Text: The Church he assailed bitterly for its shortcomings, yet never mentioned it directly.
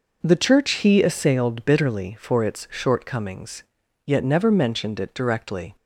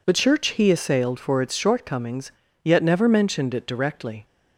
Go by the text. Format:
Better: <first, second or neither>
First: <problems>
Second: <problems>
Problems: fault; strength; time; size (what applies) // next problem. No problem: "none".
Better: first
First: none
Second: skips "bitterly"; at 1.1 s